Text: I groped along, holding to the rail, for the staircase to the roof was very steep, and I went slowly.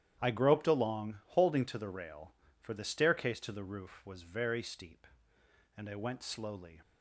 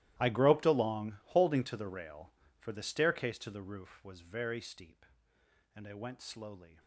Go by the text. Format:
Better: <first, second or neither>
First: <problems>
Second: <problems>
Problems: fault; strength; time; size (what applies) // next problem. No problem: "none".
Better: first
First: starts louder than the rest; strong; until 1.2 s; 10.5 dB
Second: gets quieter; strong; throughout; 19.5 dB // starts louder than the rest; strong; until 1.2 s; 15 dB